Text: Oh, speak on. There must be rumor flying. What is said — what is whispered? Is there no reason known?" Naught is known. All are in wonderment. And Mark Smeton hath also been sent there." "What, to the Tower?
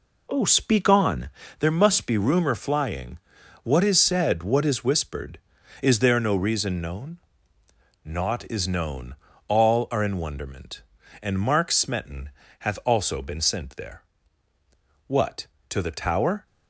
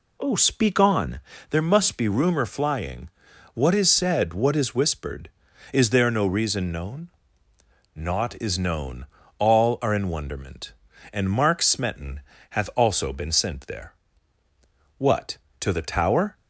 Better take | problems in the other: second | gets quieter; strong; throughout; 7.5 dB // pauses between "Smeton" and "hath"; slight; at 12.2 s; 0.30 s long; slight in the second

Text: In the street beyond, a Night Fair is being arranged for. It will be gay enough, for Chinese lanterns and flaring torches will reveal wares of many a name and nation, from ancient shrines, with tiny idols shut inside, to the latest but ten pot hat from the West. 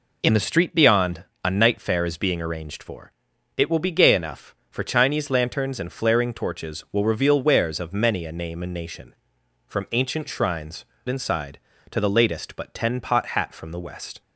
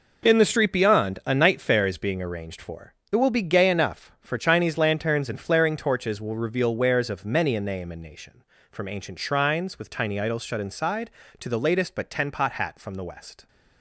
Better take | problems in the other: second | skips "with tiny idols shut"; at 10.9 s

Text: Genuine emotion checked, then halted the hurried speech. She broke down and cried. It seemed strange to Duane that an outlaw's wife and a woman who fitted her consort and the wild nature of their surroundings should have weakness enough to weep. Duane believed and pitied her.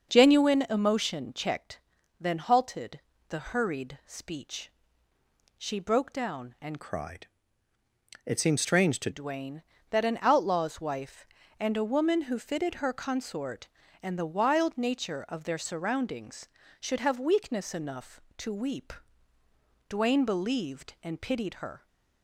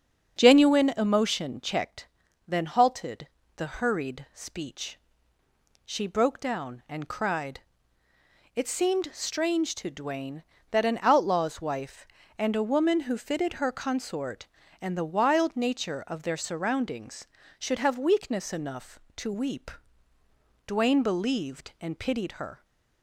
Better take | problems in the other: second | starts louder than the rest; until 1.1 s; 6.5 dB; strong in the second // pauses between "halted" and "the"; slight; at 2.9 s; 0.28 s long; slight in the second // changes voice from "cried" to "to"; from 6.8 to 9.0 s; 2.2 s long

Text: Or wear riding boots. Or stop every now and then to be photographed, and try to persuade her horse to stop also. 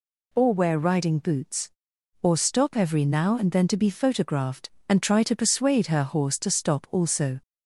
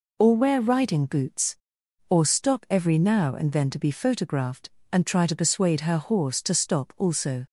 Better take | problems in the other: neither | none

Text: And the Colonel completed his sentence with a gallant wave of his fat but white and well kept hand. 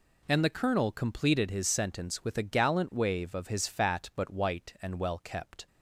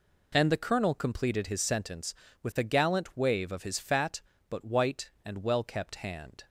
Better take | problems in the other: second | stops before "hand"; at 5.6 s

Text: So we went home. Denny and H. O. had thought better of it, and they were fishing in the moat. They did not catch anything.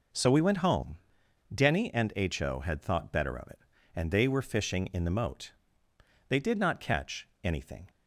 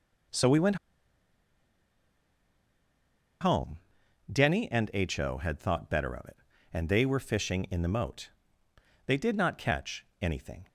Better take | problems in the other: first | pauses between "went" and "home"; strong; at 0.7 s; 2.6 s long // pauses between "catch" and "anything"; slight; at 10.0 s; 0.16 s long; slight in the first

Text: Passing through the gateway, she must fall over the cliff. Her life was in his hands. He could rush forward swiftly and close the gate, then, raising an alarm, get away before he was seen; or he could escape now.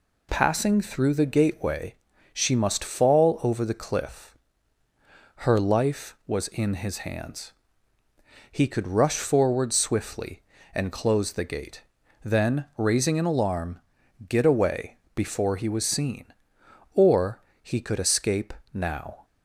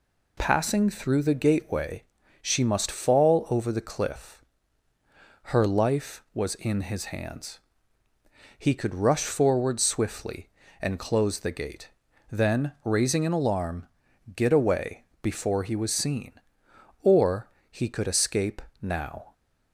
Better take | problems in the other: neither | pauses between "away" and "before"; slight; the same in both // pauses between "or" and "he"; slight; the same in both // pauses between "escape" and "now"; slight; the same in both

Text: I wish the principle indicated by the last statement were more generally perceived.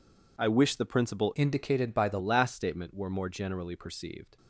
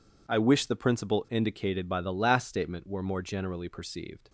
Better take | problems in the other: second | changes voice from "indicated" to "the"; from 1.3 to 2.2 s; 0.9 s long

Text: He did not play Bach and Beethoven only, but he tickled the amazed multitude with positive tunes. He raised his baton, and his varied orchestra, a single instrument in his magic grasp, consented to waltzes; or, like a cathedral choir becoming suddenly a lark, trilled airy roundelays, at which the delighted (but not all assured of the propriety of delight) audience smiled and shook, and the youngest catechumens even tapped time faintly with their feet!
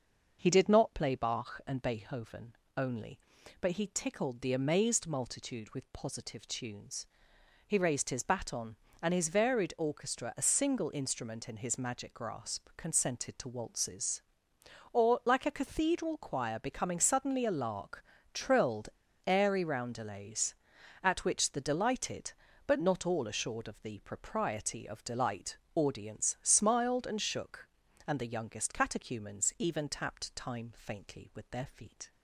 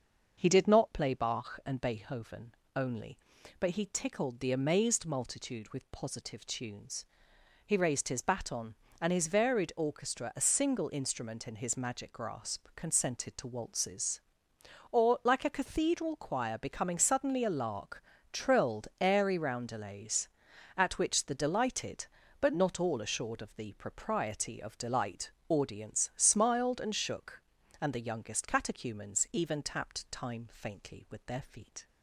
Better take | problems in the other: second | starts louder than the rest; until 1.4 s; 6.5 dB; also in the second // pauses between "Beethoven" and "only"; slight; at 2.5 s; 0.24 s long; slight in the second // pauses between "trilled" and "airy"; at 18.8 s; 0.39 s long

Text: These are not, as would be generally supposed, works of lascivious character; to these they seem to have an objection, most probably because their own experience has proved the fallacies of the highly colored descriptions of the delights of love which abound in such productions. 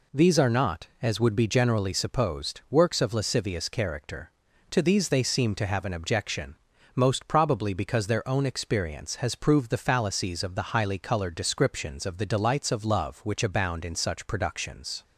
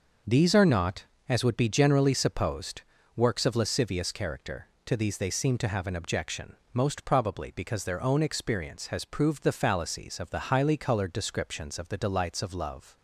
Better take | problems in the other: first | stops before "which abound in such productions"; at 12.9 s

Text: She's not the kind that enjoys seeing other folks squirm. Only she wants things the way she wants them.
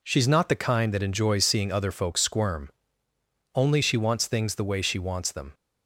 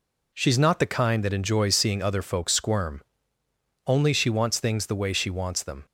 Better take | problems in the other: neither | none

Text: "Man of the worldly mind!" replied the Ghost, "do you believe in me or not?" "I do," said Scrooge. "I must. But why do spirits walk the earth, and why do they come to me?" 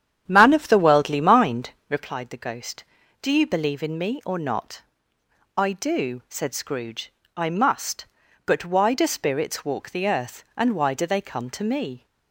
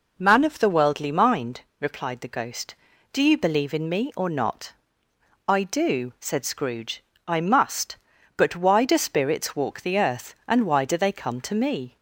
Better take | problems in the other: second | starts louder than the rest; strong; until 2.1 s; 9 dB

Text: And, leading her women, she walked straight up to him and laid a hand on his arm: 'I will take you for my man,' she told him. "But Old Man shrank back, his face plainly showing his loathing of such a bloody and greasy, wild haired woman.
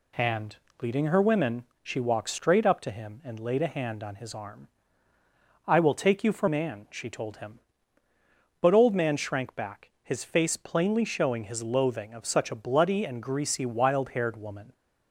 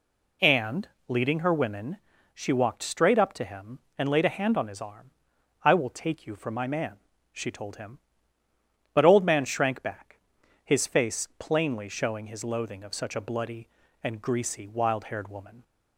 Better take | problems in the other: second | skips "my"; at 6.4 s

